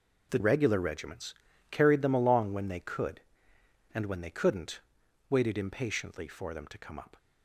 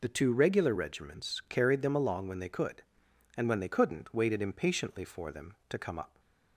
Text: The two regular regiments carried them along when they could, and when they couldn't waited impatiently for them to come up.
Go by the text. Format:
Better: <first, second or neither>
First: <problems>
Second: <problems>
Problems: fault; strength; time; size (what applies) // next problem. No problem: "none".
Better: second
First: skips "two"; at 0.3 s // pauses between "regiments" and "carried"; slight; at 1.3 s; 0.36 s long // pauses between "couldn't" and "waited"; noticeable; at 4.7 s; 0.50 s long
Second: none